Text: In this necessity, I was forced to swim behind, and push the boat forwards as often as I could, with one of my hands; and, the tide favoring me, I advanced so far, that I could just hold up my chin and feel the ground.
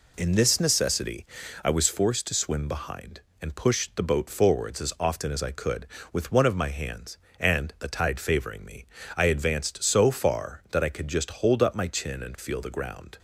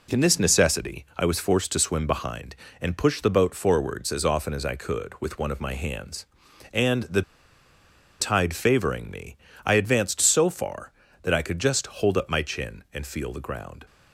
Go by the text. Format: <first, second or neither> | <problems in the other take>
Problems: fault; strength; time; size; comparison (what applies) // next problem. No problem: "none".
first | pauses between "the" and "tide"; at 7.2 s; 0.99 s long